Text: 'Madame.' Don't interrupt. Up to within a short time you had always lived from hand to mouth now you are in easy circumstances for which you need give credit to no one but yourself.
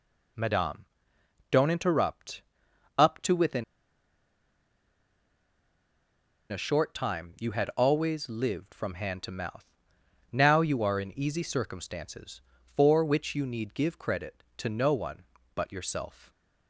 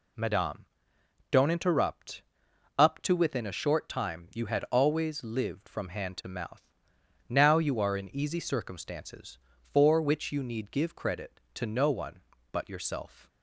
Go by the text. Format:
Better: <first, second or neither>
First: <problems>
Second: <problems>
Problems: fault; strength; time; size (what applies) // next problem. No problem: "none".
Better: second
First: pauses between "within" and "a"; strong; at 3.6 s; 2.8 s long // pauses between "mouth" and "now"; noticeable; at 9.6 s; 0.68 s long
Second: pauses between "mouth" and "now"; noticeable; at 6.6 s; 0.68 s long